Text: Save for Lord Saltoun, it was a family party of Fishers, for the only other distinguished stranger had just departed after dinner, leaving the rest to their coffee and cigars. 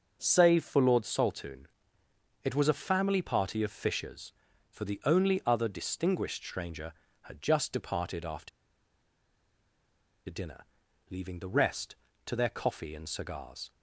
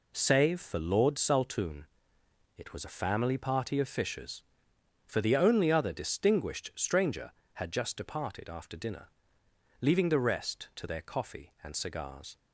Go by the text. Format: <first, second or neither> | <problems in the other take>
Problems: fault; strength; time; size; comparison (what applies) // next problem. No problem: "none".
second | starts louder than the rest; until 1.2 s; 6.5 dB // pauses between "after" and "dinner"; strong; at 8.4 s; 1.7 s long